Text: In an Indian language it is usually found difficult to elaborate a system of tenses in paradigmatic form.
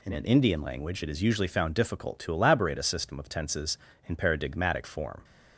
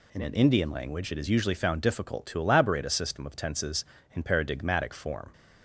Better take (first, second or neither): neither